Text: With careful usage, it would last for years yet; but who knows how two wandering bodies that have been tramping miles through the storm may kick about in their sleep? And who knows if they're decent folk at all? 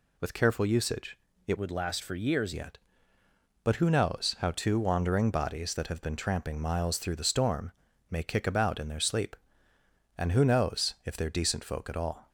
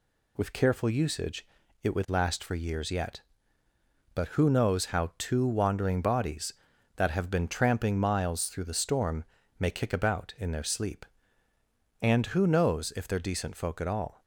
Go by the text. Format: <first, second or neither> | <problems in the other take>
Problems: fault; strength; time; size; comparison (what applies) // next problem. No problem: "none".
second | changes voice from "would" to "years"; from 1.5 to 2.5 s; 1.0 s long // pauses between "storm" and "may"; at 7.7 s; 0.40 s long; slight in the second